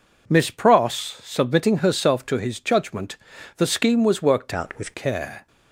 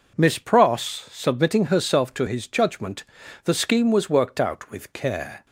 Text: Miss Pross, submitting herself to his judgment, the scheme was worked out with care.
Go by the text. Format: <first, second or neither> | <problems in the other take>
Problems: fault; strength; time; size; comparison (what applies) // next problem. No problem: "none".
second | changes voice from "out" to "with"; from 4.5 to 4.9 s; 0.4 s long